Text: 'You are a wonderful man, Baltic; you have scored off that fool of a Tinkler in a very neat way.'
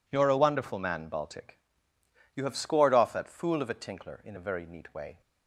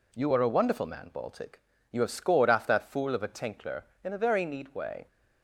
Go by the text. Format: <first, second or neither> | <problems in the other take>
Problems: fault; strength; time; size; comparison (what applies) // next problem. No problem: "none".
neither | none